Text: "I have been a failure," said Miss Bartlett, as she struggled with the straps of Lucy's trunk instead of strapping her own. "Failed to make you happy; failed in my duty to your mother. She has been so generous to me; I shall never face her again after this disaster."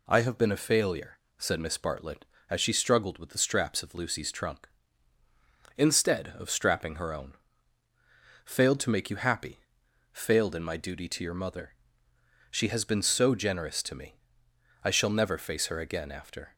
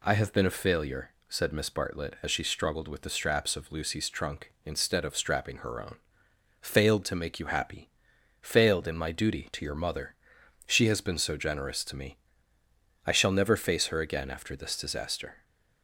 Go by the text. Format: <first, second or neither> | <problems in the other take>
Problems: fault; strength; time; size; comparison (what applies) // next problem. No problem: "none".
second | stops before "this disaster"; at 16.5 s